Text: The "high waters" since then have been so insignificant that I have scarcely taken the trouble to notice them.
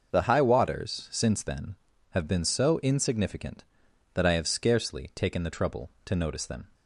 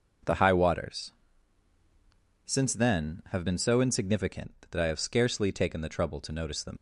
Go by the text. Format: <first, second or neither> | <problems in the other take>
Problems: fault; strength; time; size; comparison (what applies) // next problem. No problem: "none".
first | pauses between "waters" and "since"; strong; at 1.1 s; 1.3 s long // leaves "them" unfinished; at 6.7 s; 90 ms